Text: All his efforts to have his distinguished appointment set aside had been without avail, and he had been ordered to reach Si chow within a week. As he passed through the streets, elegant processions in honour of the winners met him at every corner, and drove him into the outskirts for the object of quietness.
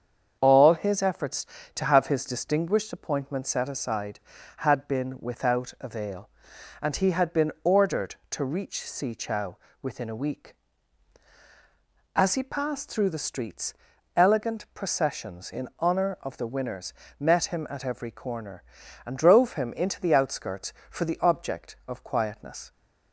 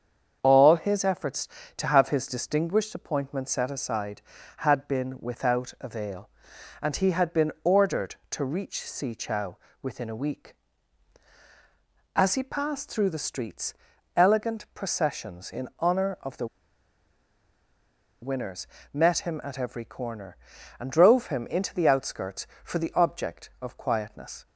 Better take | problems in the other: first | starts louder than the rest; strong; until 1.4 s; 7.5 dB; strong in the first // pauses between "chow" and "within"; slight; at 9.5 s; 0.24 s long; slight in the first // pauses between "the" and "winners"; strong; at 16.4 s; 1.7 s long // pauses between "winners" and "met"; slight; at 18.6 s; 0.26 s long; slight in the first

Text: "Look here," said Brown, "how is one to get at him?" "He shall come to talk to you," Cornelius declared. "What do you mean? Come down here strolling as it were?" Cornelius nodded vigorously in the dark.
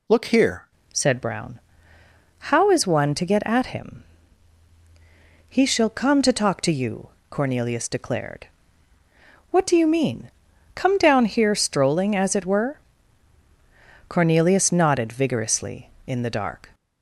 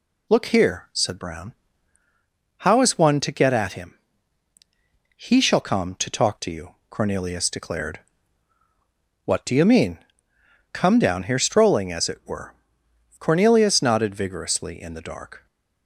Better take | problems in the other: second | changes voice at "said"; from 0.9 s on; 15.8 s long

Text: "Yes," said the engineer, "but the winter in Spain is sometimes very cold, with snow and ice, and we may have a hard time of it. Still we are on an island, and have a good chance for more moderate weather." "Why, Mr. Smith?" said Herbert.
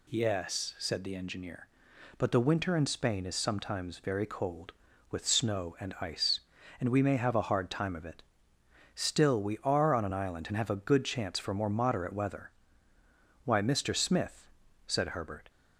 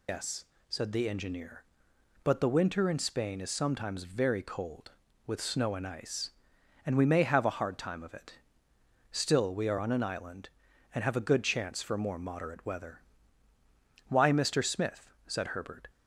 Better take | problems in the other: first | loses the start of "Yes"; at 0.0 s; 115 ms

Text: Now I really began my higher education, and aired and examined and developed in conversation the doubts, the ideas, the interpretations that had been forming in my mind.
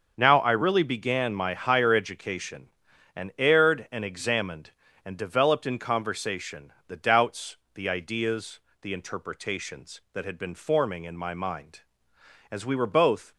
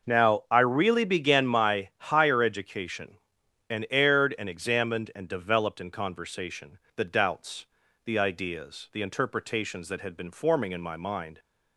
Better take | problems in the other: second | starts louder than the rest; until 1.1 s; 6.5 dB // pauses between "conversation" and "the"; slight; at 6.7 s; 0.16 s long; slight in the second // goes on to say "As we were both"; noticeable; from 12.5 s on; 0.82 s long

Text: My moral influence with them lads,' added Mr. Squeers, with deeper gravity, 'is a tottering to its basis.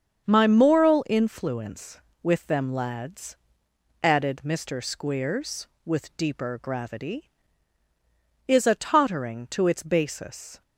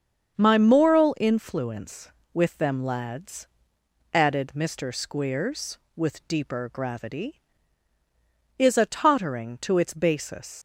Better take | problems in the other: first | starts louder than the rest; strong; until 1.4 s; 7 dB; strong in the first // leaves "basis" unfinished; at 10.5 s; 110 ms

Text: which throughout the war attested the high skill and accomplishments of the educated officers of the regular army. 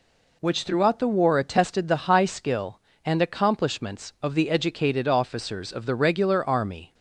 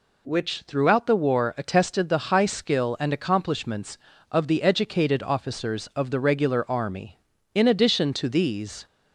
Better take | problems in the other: first | goes on to say "In addition to these"; from 7.5 s on; 1.3 s long

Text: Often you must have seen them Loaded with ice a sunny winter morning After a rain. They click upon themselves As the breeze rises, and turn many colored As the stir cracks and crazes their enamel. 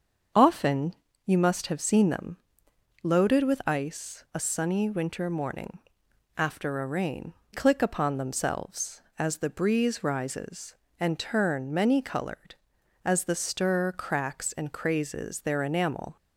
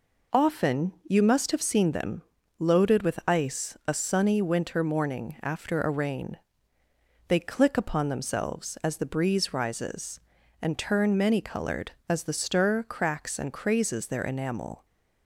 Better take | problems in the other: second | starts louder than the rest; until 1.6 s; 7 dB // pauses between "Often" and "you"; slight; at 0.9 s; 0.32 s long // pauses between "them" and "Loaded"; noticeable; at 2.3 s; 0.66 s long; slight in the second // pauses between "morning" and "After"; noticeable; at 5.7 s; 0.62 s long // skips "They"; at 7.4 s

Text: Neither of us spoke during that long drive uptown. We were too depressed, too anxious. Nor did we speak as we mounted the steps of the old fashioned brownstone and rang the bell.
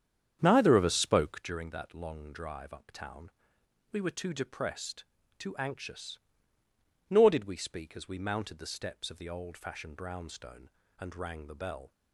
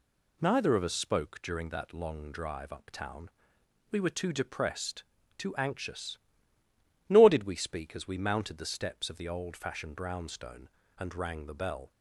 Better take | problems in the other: second | starts louder than the rest; strong; until 1.6 s; 8 dB

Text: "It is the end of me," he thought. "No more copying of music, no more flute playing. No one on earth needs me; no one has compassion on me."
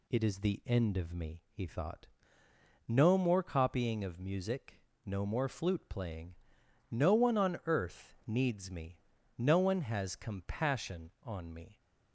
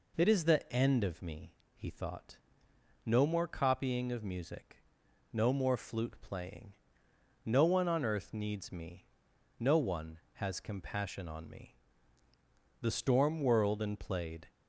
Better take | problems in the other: first | goes on to say "The storm whirled and played"; strong; from 12.7 s on; 1.6 s long

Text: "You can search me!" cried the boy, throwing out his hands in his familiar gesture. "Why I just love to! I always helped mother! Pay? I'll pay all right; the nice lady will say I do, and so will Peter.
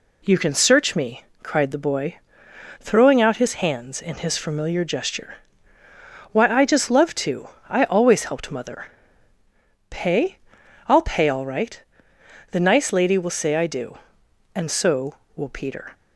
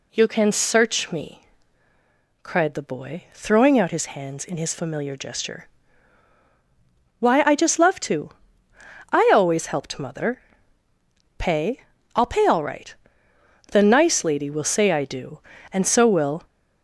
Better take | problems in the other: first | stops before "Peter"; at 16.4 s

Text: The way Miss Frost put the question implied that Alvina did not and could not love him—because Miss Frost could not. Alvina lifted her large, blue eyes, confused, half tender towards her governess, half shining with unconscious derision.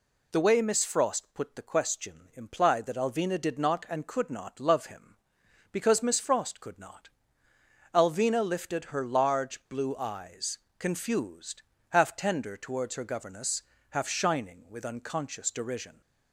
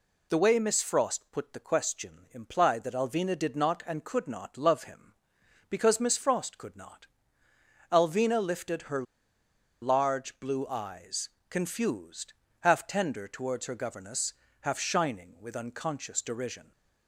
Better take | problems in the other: first | pauses between "her" and "large"; noticeable; at 9.0 s; 0.79 s long

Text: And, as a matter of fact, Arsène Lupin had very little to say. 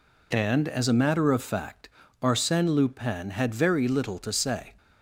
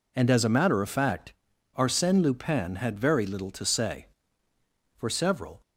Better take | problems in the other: first | goes on to say "For several"; noticeable; from 4.9 s on; 0.64 s long

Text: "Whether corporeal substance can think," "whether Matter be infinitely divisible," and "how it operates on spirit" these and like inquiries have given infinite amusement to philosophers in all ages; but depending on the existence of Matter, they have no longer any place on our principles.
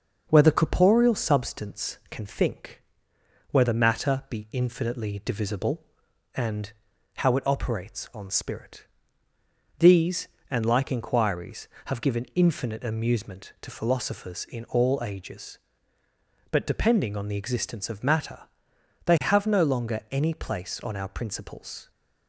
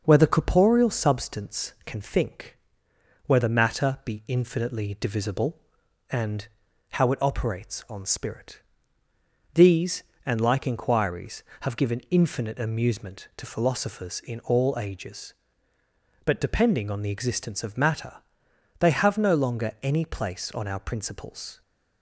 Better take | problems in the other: neither | pauses between "and" and "how"; the same in both // pauses between "spirit" and "these"; noticeable; the same in both

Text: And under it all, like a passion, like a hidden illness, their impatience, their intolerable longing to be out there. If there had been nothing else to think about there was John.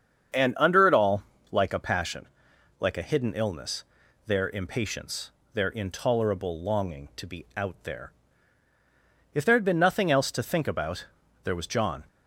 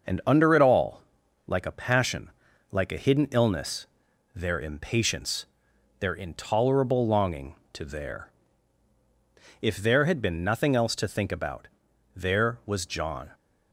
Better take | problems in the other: first | starts louder than the rest; until 1.5 s; 6 dB; strong in the first // skips "be out"; at 7.8 s // pauses between "about" and "there"; noticeable; at 11.6 s; 0.48 s long; also in the first

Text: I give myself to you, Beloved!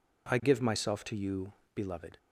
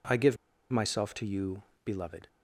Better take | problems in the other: first | pauses between "give" and "myself"; slight; at 0.3 s; 0.34 s long

